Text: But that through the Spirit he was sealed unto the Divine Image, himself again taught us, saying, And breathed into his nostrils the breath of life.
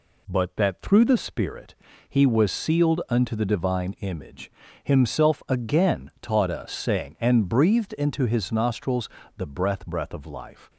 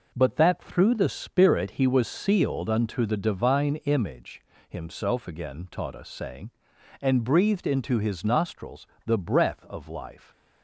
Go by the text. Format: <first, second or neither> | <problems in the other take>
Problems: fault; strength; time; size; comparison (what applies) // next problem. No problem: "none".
second | pauses between "Spirit" and "he"; slight; at 1.7 s; 0.34 s long // pauses between "nostrils" and "the"; slight; at 9.0 s; 0.28 s long; slight in the second // says "breath" twice; at 9.8 s